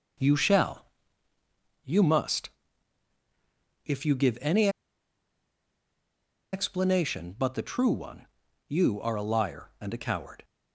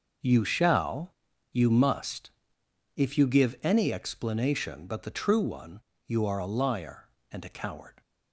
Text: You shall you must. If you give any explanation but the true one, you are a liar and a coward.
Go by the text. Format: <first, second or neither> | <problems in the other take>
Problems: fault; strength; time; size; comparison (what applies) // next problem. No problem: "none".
second | starts louder than the rest; noticeable; until 2.2 s; 6 dB // pauses between "shall" and "you"; at 0.8 s; 1.0 s long; slight in the second // pauses between "any" and "explanation"; strong; at 4.6 s; 1.8 s long